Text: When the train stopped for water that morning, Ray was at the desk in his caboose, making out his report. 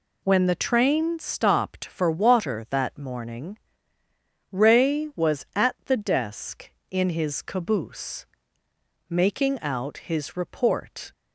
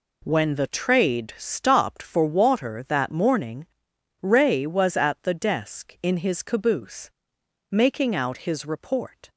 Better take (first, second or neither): first